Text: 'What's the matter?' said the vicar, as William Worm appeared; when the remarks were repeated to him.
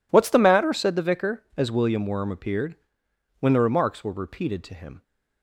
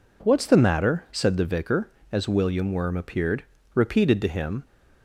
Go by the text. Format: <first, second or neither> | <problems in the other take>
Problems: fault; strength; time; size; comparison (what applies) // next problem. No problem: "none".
first | skips "when the remarks were"; at 3.5 s